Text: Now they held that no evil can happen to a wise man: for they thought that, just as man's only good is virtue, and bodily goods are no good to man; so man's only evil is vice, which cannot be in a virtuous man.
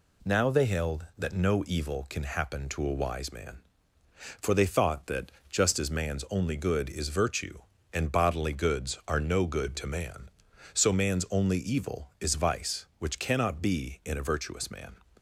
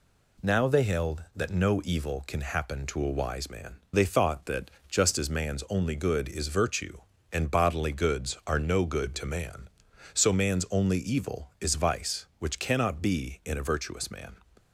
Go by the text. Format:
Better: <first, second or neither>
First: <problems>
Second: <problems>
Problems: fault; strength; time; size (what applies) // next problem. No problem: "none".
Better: first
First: none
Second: skips "for"; at 3.8 s